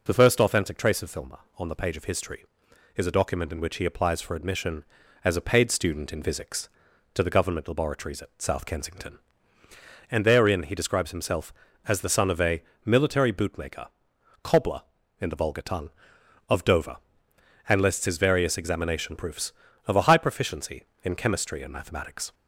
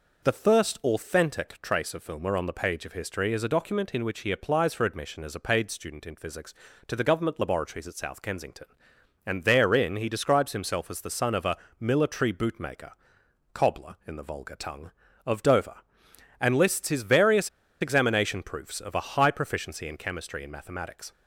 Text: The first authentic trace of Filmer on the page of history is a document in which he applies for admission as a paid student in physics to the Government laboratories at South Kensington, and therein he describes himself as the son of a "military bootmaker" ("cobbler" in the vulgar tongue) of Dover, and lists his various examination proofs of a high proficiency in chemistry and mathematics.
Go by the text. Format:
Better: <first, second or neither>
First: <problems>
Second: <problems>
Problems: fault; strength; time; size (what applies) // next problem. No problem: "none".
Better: first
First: pauses between "a" and "military"; slight; at 12.6 s; 0.24 s long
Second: pauses between "a" and "military"; slight; at 11.5 s; 0.20 s long // pauses between "various" and "examination"; slight; at 17.4 s; 0.32 s long